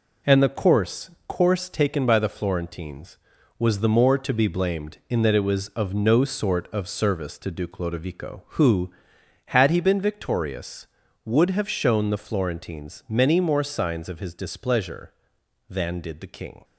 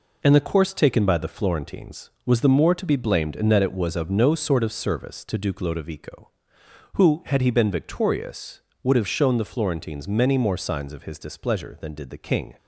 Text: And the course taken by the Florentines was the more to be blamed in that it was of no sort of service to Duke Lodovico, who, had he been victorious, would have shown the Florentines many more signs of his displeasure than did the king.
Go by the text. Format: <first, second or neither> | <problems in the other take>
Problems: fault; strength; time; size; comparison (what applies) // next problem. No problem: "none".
second | says "course" twice; at 1.2 s